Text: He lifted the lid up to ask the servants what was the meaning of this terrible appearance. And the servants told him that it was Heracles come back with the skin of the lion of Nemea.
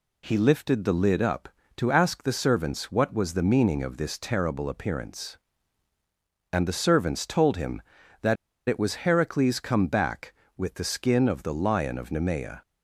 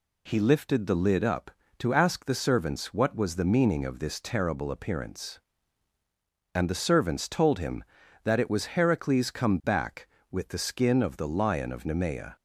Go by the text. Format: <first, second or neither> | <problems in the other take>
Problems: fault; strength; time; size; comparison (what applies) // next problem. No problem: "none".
second | pauses between "that" and "it"; slight; at 8.3 s; 0.33 s long